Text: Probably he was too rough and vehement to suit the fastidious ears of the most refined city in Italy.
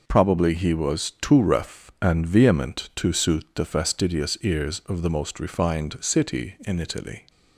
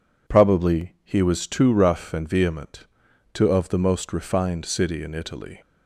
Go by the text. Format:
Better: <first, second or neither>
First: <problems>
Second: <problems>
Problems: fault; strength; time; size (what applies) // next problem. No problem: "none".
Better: first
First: none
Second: skips "suit the fastidious ears"; at 3.4 s